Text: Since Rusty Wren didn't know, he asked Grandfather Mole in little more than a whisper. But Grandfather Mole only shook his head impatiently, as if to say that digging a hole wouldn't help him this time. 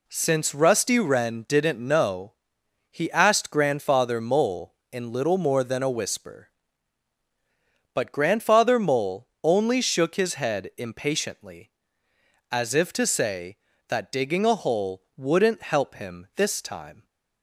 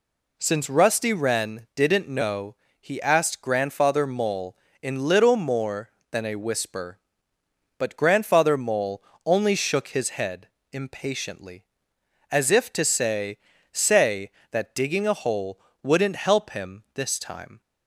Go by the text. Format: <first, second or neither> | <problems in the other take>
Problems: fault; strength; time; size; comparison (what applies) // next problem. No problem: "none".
first | pauses between "Mole" and "only"; slight; at 9.0 s; 0.22 s long // pauses between "head" and "impatiently"; slight; at 10.4 s; 0.24 s long // says "say" twice; at 13.7 s // pauses between "hole" and "wouldn't"; slight; at 15.6 s; 0.22 s long